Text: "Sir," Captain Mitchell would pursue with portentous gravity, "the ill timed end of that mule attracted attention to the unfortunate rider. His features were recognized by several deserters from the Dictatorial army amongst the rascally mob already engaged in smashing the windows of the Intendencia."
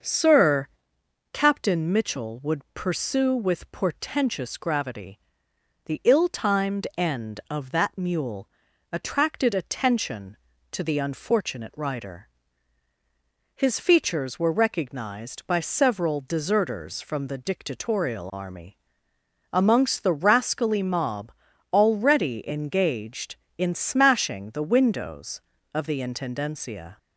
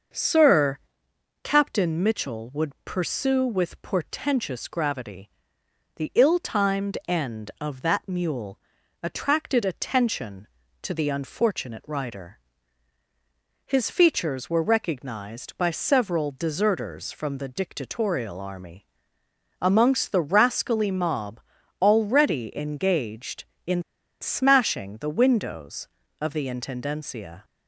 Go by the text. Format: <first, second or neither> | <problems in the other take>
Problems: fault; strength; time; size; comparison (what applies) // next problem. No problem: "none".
first | starts louder than the rest; noticeable; until 1.7 s; 6 dB; noticeable in the first // pauses between "mule" and "attracted"; at 8.5 s; 0.42 s long; also in the first // pauses between "army" and "amongst"; noticeable; at 18.8 s; 0.76 s long; noticeable in the first // pauses between "mob" and "already"; at 21.3 s; 0.40 s long; also in the first // pauses between "in" and "smashing"; at 23.8 s; 0.39 s long